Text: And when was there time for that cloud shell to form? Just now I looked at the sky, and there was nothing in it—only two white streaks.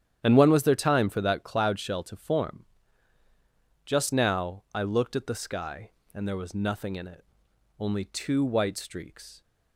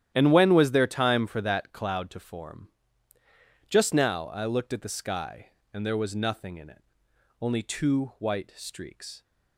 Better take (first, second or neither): first